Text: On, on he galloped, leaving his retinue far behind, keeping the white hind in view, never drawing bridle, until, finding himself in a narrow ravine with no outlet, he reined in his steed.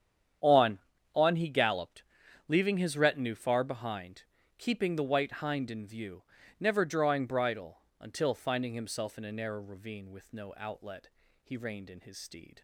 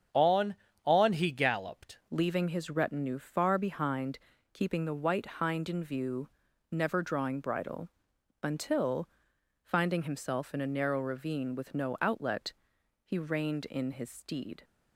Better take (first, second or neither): first